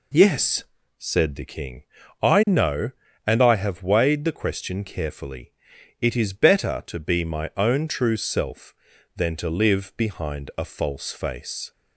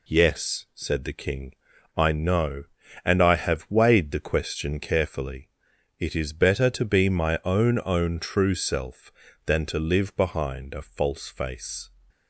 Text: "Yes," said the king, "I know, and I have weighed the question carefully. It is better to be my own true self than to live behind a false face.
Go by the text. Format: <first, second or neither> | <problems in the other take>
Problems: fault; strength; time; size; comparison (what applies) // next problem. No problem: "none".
first | says "own" twice; at 7.8 s